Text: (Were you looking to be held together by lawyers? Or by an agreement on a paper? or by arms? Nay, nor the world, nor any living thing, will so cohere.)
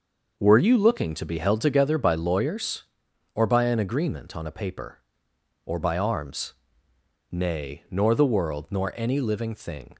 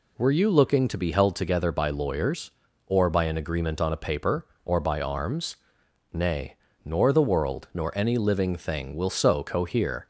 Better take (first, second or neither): second